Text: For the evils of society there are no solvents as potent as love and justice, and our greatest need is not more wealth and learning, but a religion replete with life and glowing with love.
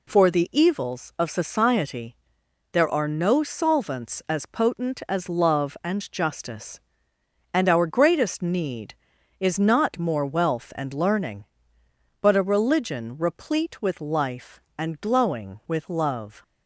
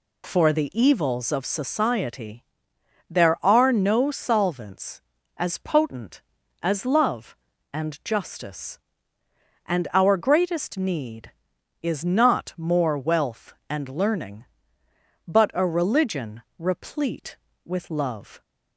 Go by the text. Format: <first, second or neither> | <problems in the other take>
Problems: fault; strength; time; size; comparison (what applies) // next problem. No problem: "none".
first | pauses between "society" and "there"; noticeable; at 2.4 s; 0.68 s long; noticeable in the first // pauses between "religion" and "replete"; slight; at 16.4 s; 0.16 s long // skips "with life and glowing"; at 17.4 s